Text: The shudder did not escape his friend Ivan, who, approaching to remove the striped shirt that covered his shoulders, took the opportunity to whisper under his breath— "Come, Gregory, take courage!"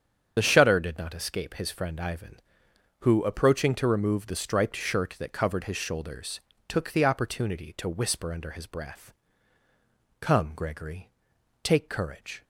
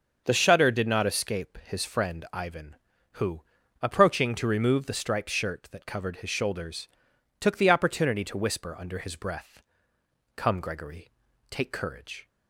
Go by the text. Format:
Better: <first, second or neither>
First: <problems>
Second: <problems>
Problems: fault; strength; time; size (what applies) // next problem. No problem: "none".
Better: second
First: loses the start of "The"; at 0.3 s; 35 ms // starts louder than the rest; strong; until 1.3 s; 7.5 dB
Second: starts louder than the rest; until 1.2 s; 6.5 dB